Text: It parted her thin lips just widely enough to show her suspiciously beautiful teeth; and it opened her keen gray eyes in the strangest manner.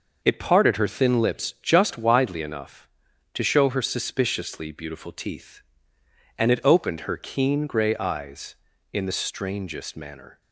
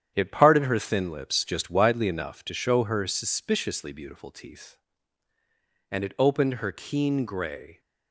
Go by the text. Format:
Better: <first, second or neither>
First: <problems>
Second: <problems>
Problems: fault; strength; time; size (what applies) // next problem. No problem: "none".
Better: first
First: none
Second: starts louder than the rest; strong; until 1.1 s; 9.5 dB // stops before "eyes in the strangest manner"; at 7.7 s